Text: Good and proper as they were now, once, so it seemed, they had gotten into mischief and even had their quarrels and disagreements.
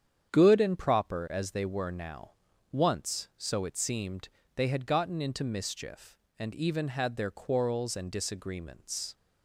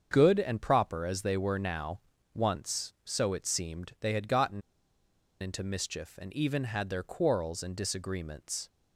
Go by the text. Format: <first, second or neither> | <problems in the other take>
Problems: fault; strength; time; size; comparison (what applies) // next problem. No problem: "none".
first | starts louder than the rest; until 1.1 s; 7 dB; strong in the first // pauses between "gotten" and "into"; noticeable; at 4.6 s; 0.80 s long